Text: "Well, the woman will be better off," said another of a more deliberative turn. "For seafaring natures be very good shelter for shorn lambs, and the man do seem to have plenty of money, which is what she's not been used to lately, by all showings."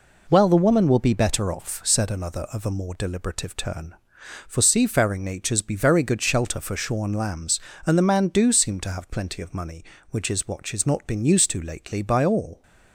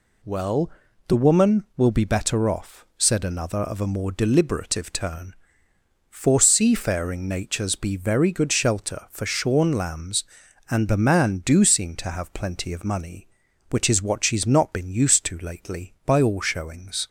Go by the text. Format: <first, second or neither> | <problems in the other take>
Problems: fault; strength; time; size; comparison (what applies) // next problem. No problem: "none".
second | stops before "showings"; at 12.6 s